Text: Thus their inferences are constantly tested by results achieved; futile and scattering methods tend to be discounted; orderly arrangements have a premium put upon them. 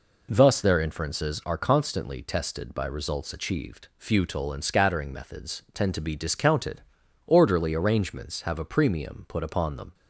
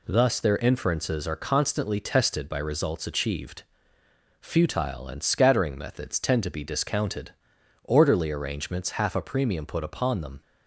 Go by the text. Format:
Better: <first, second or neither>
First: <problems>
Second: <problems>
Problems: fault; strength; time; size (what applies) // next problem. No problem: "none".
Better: first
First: none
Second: says "half" for "have"; at 9.0 s